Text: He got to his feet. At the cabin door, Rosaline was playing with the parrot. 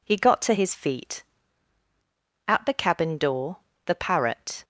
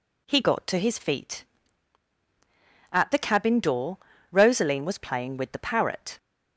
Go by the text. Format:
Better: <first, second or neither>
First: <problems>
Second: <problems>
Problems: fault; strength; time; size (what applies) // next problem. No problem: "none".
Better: second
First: skips "Rosaline was playing with"; at 3.7 s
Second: none